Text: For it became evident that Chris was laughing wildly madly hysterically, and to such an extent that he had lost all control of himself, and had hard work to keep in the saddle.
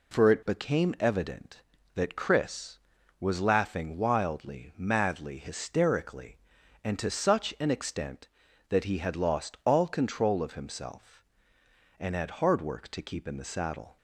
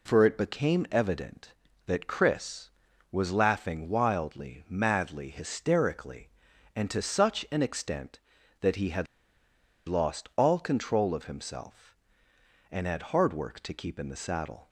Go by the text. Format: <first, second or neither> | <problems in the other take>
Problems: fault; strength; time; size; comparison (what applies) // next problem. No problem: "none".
first | pauses between "had" and "lost"; noticeable; at 9.0 s; 0.82 s long